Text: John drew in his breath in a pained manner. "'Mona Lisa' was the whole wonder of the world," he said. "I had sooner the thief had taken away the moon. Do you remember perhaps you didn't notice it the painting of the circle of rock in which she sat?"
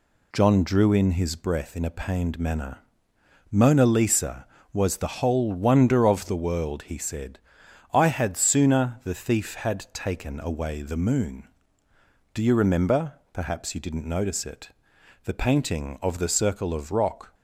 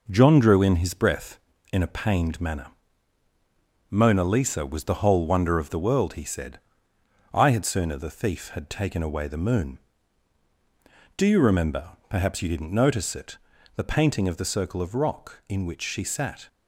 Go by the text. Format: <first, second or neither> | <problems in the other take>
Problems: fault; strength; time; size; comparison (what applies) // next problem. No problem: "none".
second | pauses between "remember" and "perhaps"; slight; at 13.1 s; 0.20 s long; slight in the second // pauses between "it" and "the"; noticeable; at 14.6 s; 0.56 s long; also in the second // stops before "in which she sat"; at 17.3 s